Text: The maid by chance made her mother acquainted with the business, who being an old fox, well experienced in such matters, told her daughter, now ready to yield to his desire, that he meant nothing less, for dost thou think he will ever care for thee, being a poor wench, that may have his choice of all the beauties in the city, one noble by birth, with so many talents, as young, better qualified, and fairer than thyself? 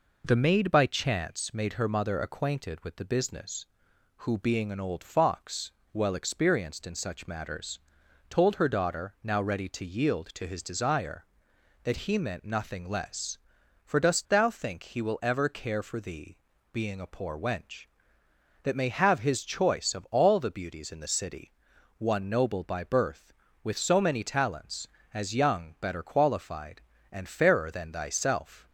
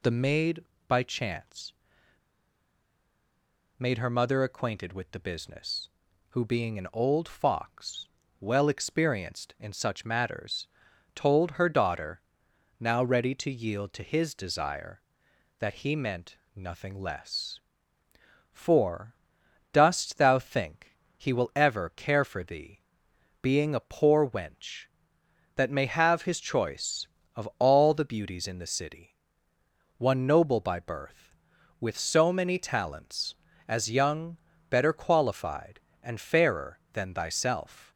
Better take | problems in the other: first | pauses between "chance" and "made"; strong; at 1.7 s; 2.0 s long // pauses between "meant" and "nothing"; slight; at 16.3 s; 0.18 s long // pauses between "for" and "dost"; noticeable; at 19.1 s; 0.58 s long // pauses between "think" and "he"; slight; at 20.9 s; 0.18 s long

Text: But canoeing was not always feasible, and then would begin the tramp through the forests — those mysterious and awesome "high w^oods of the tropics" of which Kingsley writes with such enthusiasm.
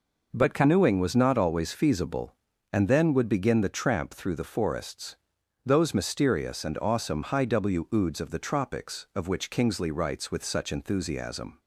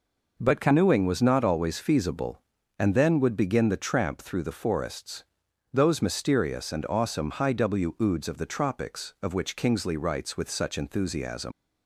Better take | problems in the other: first | leaves "enthusiasm" unfinished; at 11.5 s; 135 ms

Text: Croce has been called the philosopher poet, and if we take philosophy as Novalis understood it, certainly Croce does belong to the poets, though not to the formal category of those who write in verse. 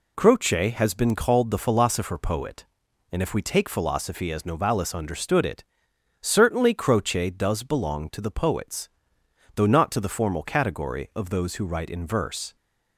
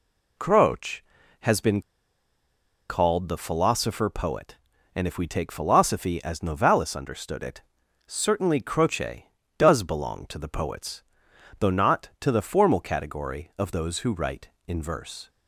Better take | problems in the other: first | pauses between "been" and "called"; at 1.8 s; 1.0 s long

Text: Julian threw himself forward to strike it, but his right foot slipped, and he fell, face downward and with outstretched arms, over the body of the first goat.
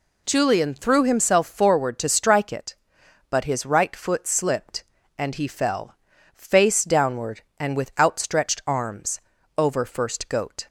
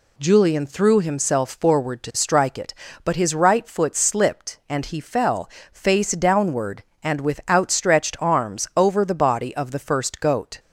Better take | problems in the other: second | skips "the body of the"; at 9.8 s

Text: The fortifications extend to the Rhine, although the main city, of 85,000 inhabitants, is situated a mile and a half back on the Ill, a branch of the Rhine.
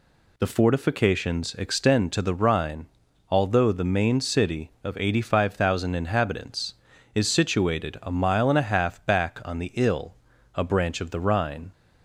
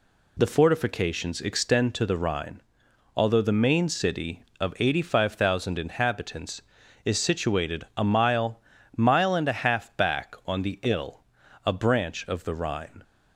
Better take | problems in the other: first | says "mile" twice; at 8.9 s

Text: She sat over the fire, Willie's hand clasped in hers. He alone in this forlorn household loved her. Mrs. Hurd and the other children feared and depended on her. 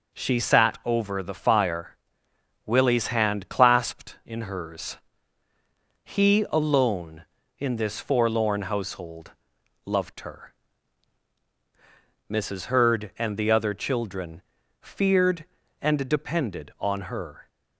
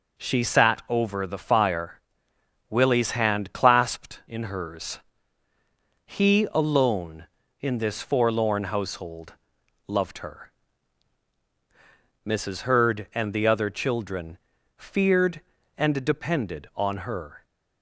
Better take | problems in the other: neither | pauses between "household" and "loved"; noticeable; the same in both // pauses between "children" and "feared"; the same in both

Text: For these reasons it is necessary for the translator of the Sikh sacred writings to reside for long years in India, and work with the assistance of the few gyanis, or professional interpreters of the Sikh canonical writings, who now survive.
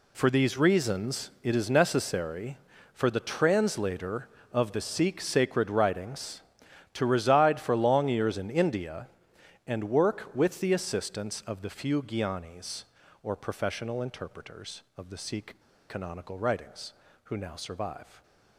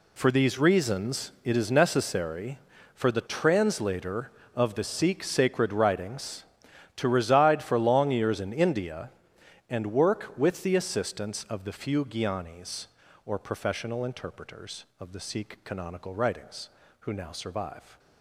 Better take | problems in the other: second | pauses between "Sikh" and "canonical"; slight; at 15.5 s; 0.28 s long

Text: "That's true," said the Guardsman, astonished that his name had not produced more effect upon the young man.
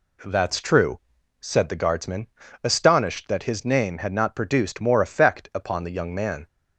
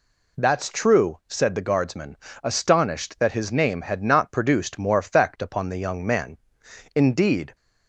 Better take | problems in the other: first | goes on to say "Indeed"; noticeable; from 6.9 s on; 0.62 s long

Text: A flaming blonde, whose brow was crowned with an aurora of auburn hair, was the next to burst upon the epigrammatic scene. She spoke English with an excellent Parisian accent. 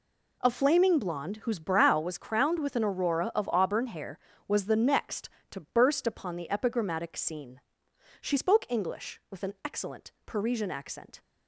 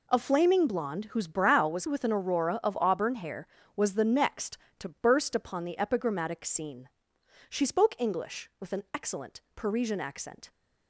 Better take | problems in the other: first | skips "crowned"; at 1.8 s // pauses between "excellent" and "Parisian"; slight; at 9.4 s; 0.16 s long; slight in the first

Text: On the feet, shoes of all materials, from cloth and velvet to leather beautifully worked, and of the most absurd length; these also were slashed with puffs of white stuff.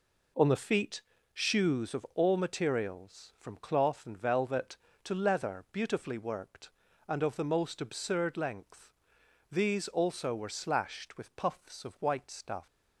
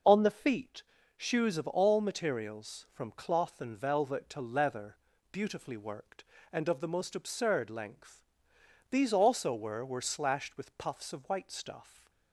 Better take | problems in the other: first | pauses between "leather" and "beautifully"; slight; at 4.9 s; 0.34 s long // says "were" twice; at 9.8 s

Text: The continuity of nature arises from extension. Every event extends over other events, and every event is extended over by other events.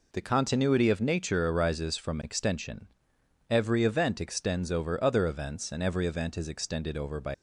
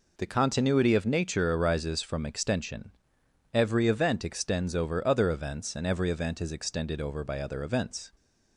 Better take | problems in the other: second | stops before "other events"; at 7.3 s

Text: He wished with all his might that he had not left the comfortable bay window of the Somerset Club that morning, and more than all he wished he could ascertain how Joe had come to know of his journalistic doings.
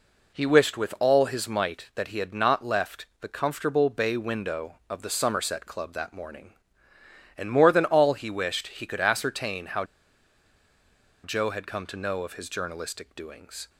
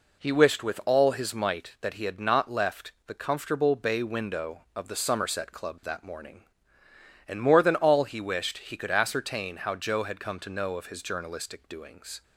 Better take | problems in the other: second | pauses between "how" and "Joe"; strong; at 9.8 s; 1.3 s long

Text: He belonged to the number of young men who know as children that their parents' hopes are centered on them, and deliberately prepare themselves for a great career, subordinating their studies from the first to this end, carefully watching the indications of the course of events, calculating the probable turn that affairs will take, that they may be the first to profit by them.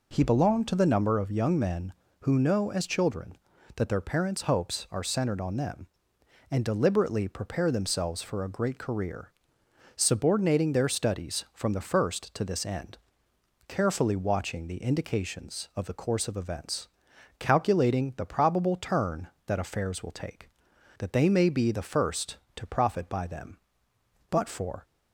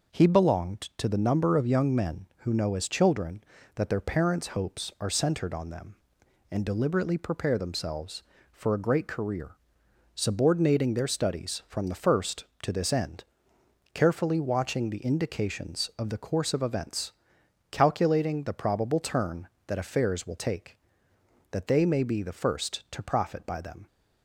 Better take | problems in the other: second | goes on to say "But for"; from 24.2 s on; 0.54 s long

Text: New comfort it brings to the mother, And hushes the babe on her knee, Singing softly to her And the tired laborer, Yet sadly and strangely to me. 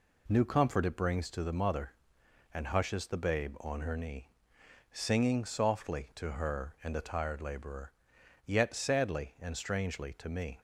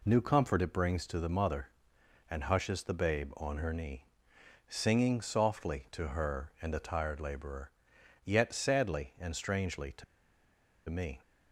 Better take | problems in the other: first | pauses between "to" and "me"; noticeable; at 10.0 s; 0.86 s long

